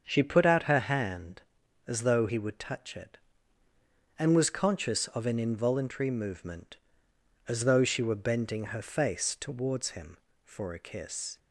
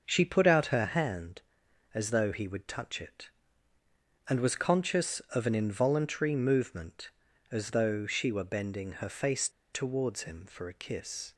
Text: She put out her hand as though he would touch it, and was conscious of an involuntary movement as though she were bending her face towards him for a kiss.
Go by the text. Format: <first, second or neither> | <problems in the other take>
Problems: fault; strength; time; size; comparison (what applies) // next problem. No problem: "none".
first | starts louder than the rest; noticeable; until 1.0 s; 6 dB; also in the first // pauses between "face" and "towards"; slight; at 9.4 s; 0.23 s long